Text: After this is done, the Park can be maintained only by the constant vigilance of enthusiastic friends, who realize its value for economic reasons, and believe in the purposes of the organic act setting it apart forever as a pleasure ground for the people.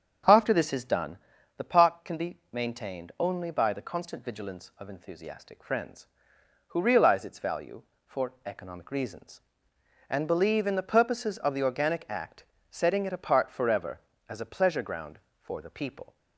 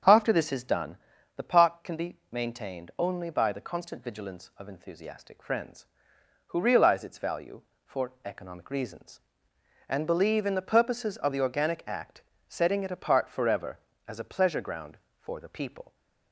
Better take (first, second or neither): neither